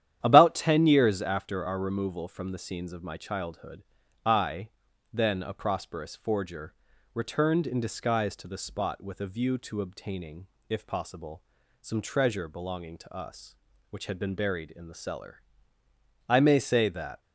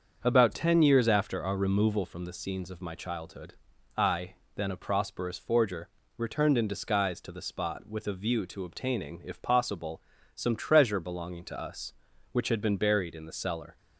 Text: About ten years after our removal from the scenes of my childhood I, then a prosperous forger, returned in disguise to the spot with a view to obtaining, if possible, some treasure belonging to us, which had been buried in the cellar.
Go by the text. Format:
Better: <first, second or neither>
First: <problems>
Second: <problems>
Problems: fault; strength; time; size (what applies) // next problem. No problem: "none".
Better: second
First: starts louder than the rest; strong; until 1.2 s; 10.5 dB // pauses between "childhood" and "I"; at 3.8 s; 0.40 s long // goes on to say "I may say that"; noticeable; from 16.2 s on; 0.92 s long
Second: starts louder than the rest; until 1.2 s; 7 dB // pauses between "childhood" and "I"; at 3.5 s; 0.42 s long